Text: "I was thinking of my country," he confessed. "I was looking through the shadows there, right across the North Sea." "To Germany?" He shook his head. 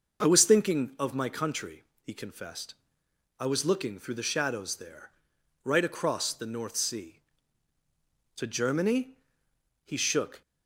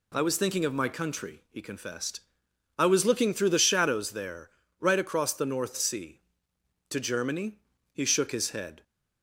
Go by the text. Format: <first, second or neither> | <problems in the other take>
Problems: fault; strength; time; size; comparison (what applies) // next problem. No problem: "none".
second | stops before "his head"; at 10.4 s